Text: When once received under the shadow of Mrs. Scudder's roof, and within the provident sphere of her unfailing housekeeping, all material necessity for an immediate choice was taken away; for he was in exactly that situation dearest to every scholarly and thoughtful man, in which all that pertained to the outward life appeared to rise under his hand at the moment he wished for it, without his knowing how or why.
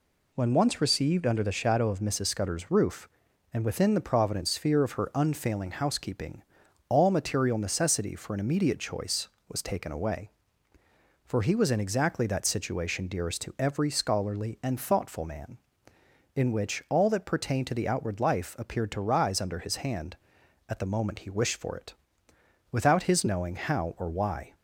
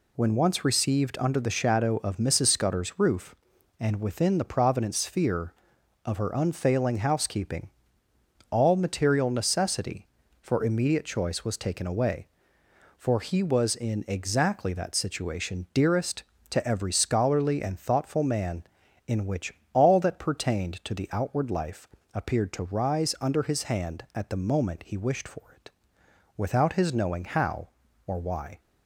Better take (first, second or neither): first